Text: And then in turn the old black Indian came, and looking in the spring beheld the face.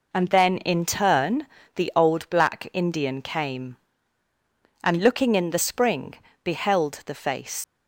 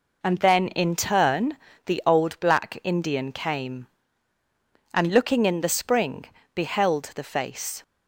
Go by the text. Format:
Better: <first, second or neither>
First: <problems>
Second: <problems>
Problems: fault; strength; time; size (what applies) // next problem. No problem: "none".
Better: second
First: pauses between "turn" and "the"; slight; at 1.4 s; 0.28 s long // pauses between "spring" and "beheld"; slight; at 6.1 s; 0.28 s long // leaves "face" unfinished; at 7.6 s; 95 ms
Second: pauses between "turn" and "the"; slight; at 1.5 s; 0.28 s long // pauses between "spring" and "beheld"; slight; at 6.2 s; 0.28 s long